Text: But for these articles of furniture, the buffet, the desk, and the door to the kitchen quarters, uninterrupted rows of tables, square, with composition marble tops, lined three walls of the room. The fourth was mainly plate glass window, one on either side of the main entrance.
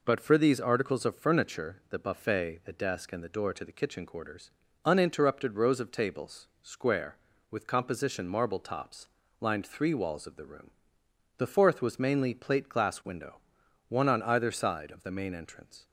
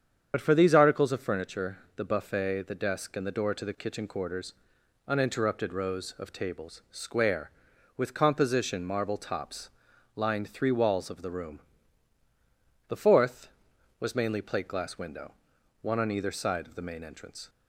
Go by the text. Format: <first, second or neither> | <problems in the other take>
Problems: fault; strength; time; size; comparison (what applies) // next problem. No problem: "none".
first | loses the start of "But"; at 0.3 s; 55 ms // starts louder than the rest; strong; until 1.3 s; 8 dB